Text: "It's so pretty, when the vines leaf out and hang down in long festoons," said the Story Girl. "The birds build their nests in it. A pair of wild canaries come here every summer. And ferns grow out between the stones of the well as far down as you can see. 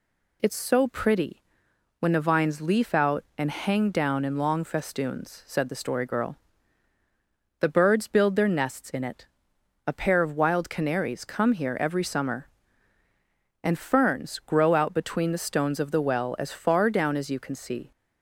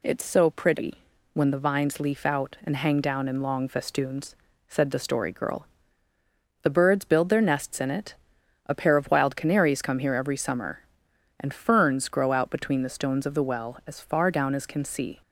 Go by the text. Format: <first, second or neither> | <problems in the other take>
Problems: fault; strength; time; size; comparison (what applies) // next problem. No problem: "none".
first | skips "you"; at 14.6 s